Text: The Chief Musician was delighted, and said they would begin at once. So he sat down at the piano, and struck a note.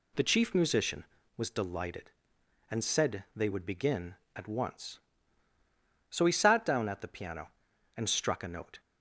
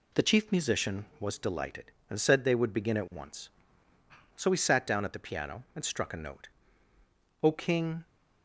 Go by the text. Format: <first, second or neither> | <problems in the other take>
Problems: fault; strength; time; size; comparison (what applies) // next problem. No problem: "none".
first | goes on to say "O King"; noticeable; from 7.4 s on; 0.64 s long